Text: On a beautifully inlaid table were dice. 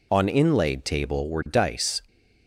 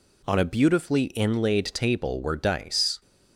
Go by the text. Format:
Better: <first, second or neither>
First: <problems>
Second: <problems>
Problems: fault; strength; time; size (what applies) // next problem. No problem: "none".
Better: second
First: skips "a beautifully"; at 0.2 s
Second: none